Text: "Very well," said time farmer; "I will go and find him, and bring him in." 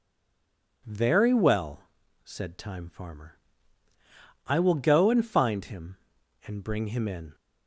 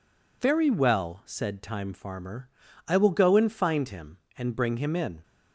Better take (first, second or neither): second